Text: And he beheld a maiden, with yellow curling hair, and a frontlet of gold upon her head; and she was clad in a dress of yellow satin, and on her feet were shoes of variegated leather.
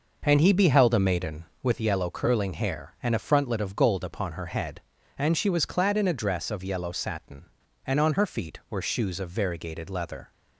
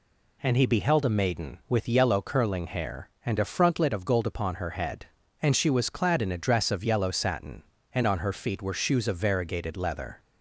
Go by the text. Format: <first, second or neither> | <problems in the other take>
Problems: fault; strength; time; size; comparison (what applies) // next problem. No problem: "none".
second | starts louder than the rest; noticeable; until 1.8 s; 5.5 dB